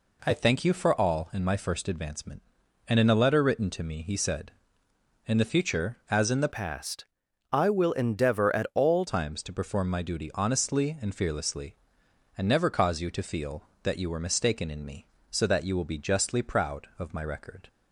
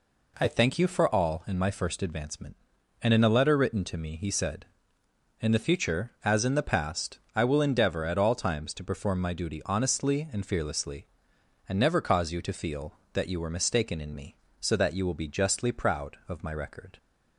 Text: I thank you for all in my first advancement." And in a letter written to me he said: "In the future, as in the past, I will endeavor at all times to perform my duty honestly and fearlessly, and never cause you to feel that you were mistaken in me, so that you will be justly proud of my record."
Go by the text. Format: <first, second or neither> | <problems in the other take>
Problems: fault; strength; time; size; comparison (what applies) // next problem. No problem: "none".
second | changes voice from "past" to "all"; from 6.5 to 9.0 s; 2.5 s long